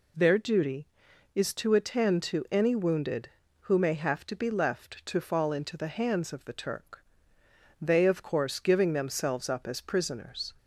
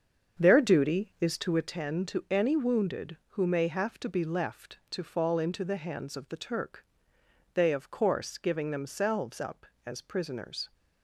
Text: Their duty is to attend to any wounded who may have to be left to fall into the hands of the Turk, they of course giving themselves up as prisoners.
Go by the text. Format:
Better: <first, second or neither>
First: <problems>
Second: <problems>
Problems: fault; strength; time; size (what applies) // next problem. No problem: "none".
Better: first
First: none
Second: starts louder than the rest; strong; until 1.8 s; 7 dB